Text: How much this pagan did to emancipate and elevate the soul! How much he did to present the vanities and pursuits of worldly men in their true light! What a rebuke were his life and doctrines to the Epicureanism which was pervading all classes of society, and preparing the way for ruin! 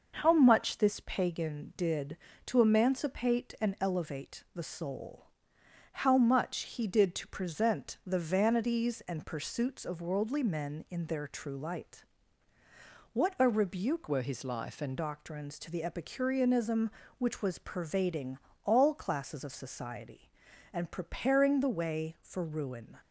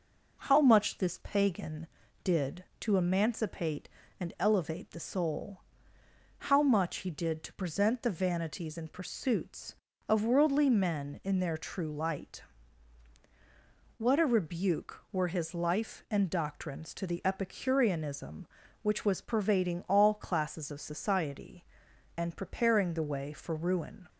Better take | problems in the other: second | changes voice from "were" to "and"; from 14.0 to 14.9 s; 0.9 s long // pauses between "pervading" and "all"; slight; at 18.3 s; 0.26 s long

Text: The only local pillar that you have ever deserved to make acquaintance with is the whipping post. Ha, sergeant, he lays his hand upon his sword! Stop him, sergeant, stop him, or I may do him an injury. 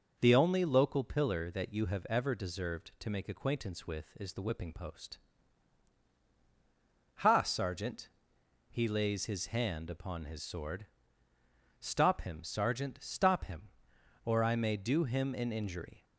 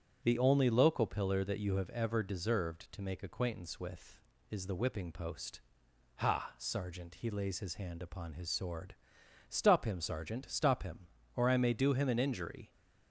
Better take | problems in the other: neither | none

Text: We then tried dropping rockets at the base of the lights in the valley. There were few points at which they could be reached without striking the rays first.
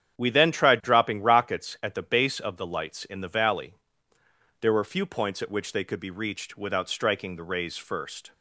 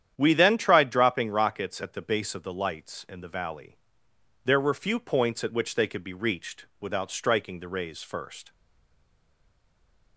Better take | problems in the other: first | starts louder than the rest; strong; until 1.1 s; 9.5 dB; strong in the first // stays silent after the last word; noticeable; from 8.5 s on; 1.6 s long

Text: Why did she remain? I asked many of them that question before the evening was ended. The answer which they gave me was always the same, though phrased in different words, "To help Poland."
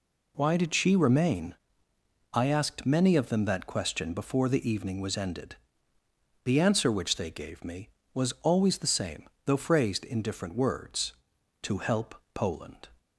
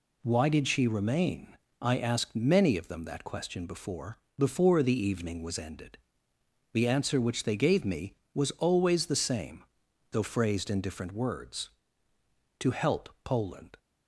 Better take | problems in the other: first | says "before" twice; at 4.3 s // pauses between "help" and "Poland"; slight; at 13.0 s; 0.16 s long; slight in the first

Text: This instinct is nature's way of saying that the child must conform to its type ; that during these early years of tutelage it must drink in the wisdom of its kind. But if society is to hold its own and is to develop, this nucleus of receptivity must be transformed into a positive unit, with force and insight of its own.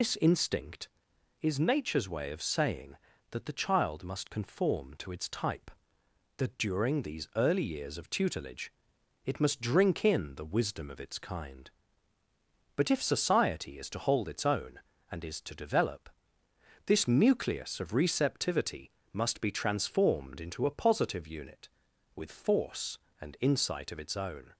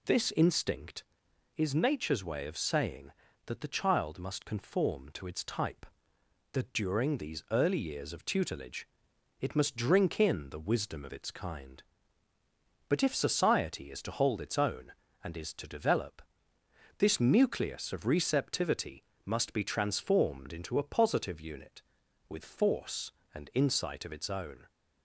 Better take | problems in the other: second | loses the start of "This"; at 0.0 s; 95 ms // pauses between "tutelage" and "it"; noticeable; at 8.7 s; 0.52 s long; noticeable in the second // pauses between "receptivity" and "must"; slight; at 18.9 s; 0.22 s long; slight in the second

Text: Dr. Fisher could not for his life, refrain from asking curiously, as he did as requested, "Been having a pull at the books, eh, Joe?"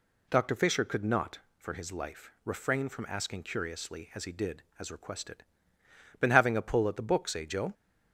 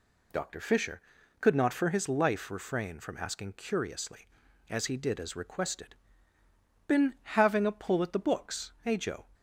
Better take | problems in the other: neither | none

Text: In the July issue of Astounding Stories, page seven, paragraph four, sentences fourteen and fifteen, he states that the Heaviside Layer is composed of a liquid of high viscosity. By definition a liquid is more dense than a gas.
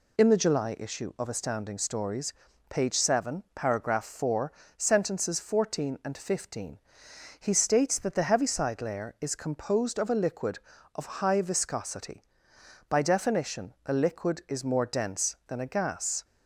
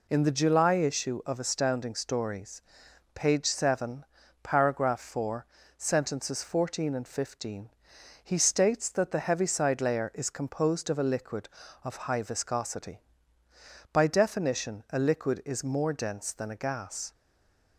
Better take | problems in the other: first | stays silent after the last word; slight; from 17.1 s on; 0.6 s long

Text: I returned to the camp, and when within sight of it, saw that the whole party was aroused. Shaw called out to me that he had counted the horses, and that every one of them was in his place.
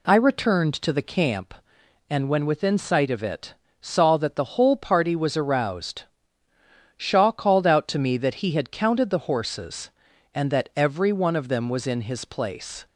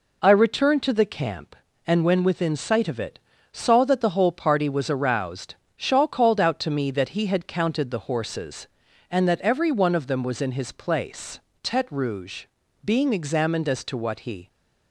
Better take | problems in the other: first | goes on to say "Tete Rouge being examined as to what he"; strong; from 11.6 s on; 2.8 s long

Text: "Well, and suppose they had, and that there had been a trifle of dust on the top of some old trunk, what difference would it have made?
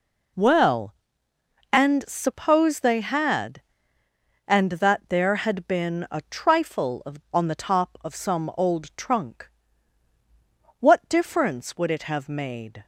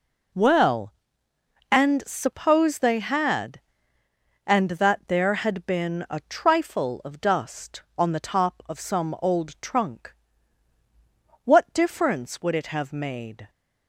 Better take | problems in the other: second | skips "dust"; at 7.2 s

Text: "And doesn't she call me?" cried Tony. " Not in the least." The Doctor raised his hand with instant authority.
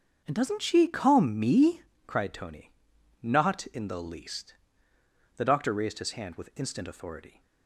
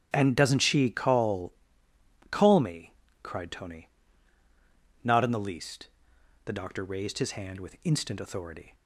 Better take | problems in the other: first | starts louder than the rest; strong; until 1.1 s; 7.5 dB; strong in the first // says "call" twice; at 2.3 s

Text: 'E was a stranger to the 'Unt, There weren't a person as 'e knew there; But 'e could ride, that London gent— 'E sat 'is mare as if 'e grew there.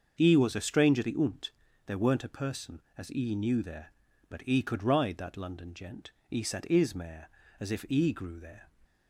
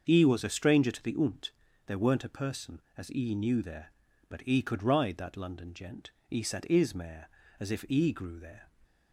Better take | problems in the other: second | starts louder than the rest; until 1.2 s; 6.5 dB; also in the second // skips "to"; at 1.0 s

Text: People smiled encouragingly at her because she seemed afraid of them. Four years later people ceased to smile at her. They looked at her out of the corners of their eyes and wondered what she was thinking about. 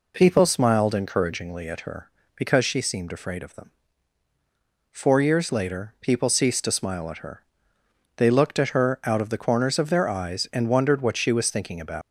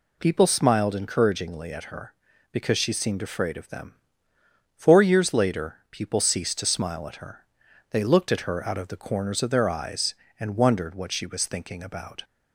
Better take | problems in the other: second | leaves "about" unfinished; at 12.0 s; 140 ms

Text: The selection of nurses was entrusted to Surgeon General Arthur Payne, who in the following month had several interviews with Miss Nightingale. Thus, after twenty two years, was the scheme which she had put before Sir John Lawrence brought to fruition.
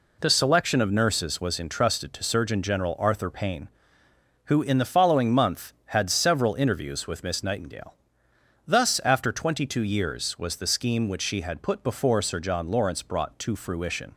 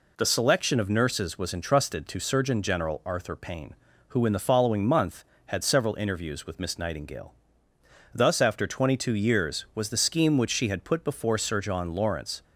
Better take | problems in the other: first | stops before "brought to fruition"; at 12.4 s

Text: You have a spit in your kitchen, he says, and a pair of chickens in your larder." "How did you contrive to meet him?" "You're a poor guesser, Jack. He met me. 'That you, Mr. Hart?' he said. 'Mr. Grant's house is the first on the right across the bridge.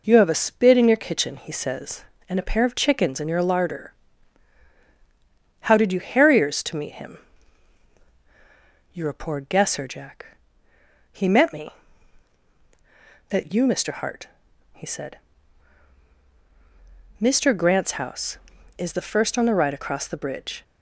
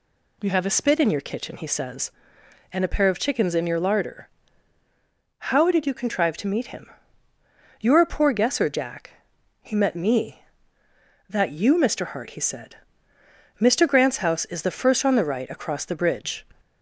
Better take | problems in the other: second | says "harriers" for "contrive"; at 5.9 s

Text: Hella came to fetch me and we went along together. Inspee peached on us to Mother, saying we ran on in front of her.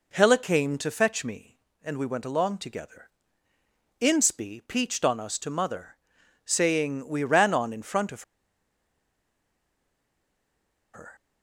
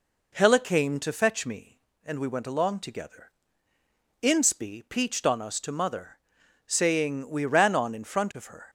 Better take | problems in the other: second | pauses between "of" and "her"; strong; at 8.2 s; 2.7 s long

